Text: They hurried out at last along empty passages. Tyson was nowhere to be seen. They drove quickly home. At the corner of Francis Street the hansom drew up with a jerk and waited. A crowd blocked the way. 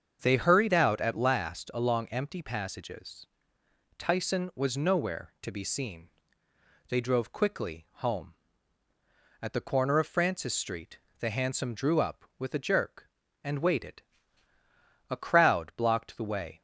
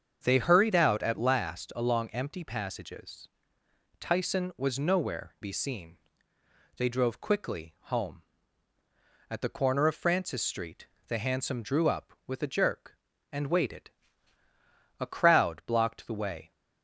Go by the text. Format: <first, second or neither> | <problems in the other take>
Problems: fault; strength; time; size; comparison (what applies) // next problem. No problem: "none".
first | starts louder than the rest; strong; until 1.2 s; 7 dB; strong in the first // skips "to"; at 5.3 s // pauses between "Street" and "the"; slight; at 10.8 s; 0.20 s long; slight in the first